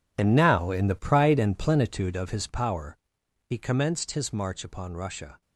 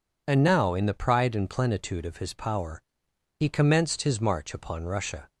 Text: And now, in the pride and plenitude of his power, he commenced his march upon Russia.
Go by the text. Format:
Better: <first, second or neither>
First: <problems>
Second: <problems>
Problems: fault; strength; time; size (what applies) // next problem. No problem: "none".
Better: second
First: gets quieter; strong; throughout; 14 dB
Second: none